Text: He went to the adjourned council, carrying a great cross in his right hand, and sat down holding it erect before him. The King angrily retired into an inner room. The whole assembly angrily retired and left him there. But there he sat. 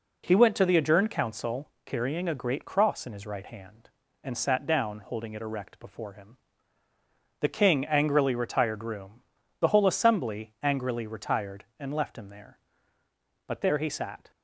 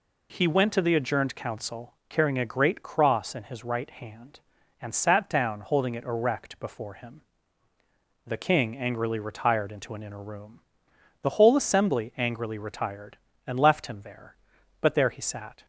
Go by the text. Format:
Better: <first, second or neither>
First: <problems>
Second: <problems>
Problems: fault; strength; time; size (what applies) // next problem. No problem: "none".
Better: second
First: skips "into an inner"; at 8.8 s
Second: none